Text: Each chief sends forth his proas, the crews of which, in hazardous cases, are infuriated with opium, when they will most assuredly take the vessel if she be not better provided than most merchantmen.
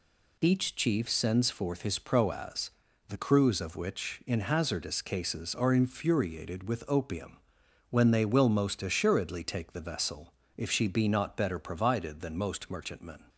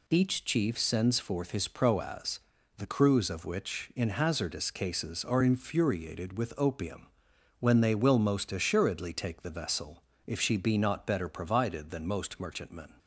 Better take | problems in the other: neither | pauses between "vessel" and "if"; slight; the same in both

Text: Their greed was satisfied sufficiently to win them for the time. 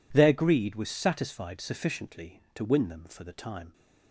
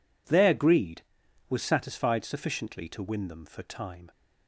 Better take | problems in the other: first | skips "the"; at 3.6 s

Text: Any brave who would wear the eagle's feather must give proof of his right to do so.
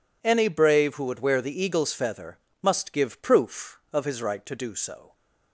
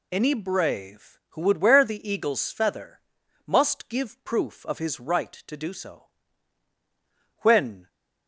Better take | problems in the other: first | pauses between "feather" and "must"; at 3.0 s; 0.44 s long; slight in the first // goes on to say "When"; from 7.3 s on; 0.50 s long

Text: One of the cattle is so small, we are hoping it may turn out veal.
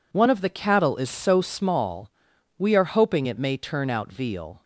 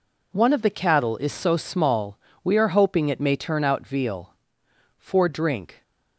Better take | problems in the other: first | goes on to say "For drink"; noticeable; from 4.9 s on; 0.84 s long

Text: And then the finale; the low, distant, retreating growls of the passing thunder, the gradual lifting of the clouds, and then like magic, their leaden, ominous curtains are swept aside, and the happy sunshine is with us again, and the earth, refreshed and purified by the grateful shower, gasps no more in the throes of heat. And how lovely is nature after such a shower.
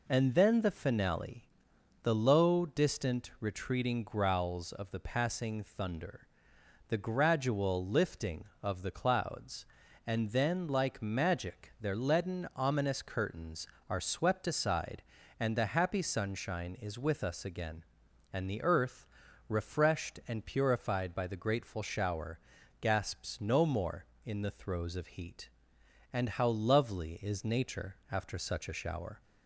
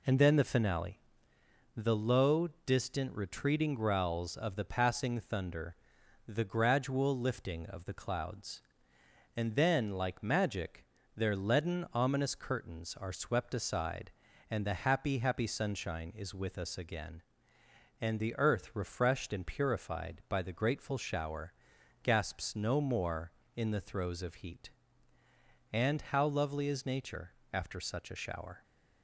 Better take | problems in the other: first | says "happy" twice; at 15.1 s // pauses between "nature" and "after"; slight; at 27.3 s; 0.22 s long; slight in the first

